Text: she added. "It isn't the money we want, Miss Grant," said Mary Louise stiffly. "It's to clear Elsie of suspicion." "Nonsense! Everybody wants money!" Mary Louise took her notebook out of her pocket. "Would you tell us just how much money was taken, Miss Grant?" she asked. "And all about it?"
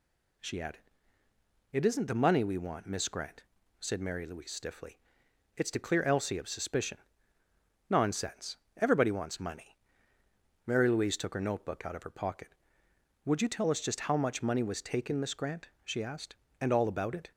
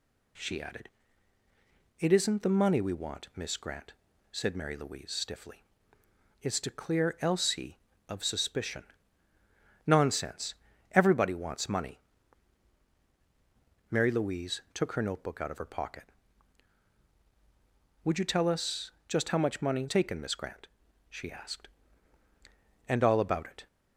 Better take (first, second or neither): first